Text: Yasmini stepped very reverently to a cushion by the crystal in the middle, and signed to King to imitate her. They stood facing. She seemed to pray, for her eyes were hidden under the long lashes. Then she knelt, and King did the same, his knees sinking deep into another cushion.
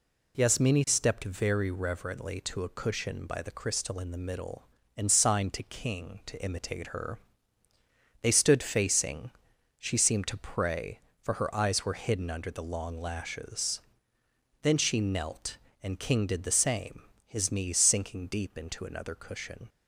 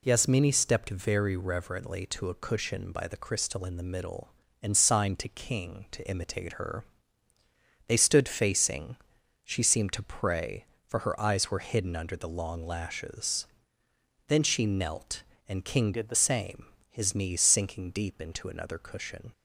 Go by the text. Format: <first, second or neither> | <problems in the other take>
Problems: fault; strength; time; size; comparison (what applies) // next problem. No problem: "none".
first | changes voice from "did" to "the"; from 15.9 to 16.1 s; 0.2 s long